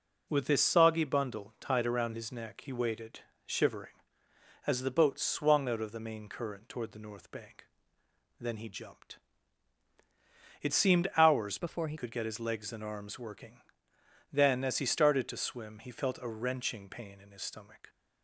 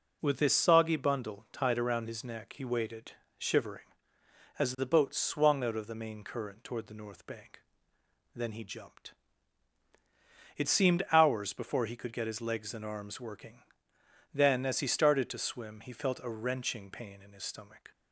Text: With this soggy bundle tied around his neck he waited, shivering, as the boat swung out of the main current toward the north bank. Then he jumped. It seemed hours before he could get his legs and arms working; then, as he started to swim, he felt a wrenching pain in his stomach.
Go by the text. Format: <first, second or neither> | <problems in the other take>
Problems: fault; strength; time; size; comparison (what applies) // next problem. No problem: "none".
second | changes voice from "before" to "he"; from 11.5 to 11.9 s; 0.4 s long